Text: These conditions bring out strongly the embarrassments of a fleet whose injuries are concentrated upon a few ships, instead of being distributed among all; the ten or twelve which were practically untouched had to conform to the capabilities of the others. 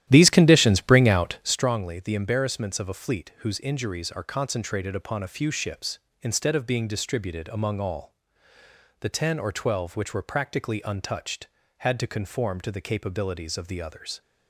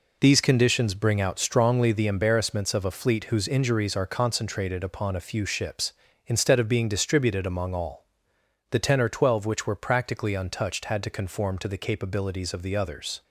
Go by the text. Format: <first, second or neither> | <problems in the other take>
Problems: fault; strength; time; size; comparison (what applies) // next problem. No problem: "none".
second | starts louder than the rest; strong; until 1.7 s; 12.5 dB